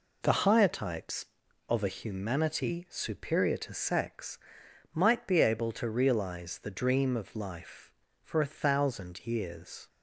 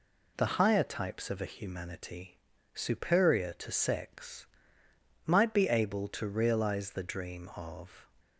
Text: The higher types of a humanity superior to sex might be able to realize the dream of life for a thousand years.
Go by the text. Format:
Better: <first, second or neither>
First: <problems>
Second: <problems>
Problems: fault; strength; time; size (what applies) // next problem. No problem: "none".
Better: first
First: pauses between "sex" and "might"; noticeable; at 4.3 s; 0.56 s long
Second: pauses between "humanity" and "superior"; slight; at 2.3 s; 0.34 s long // pauses between "sex" and "might"; noticeable; at 4.4 s; 0.80 s long // stops before "life for a thousand years"; at 8.2 s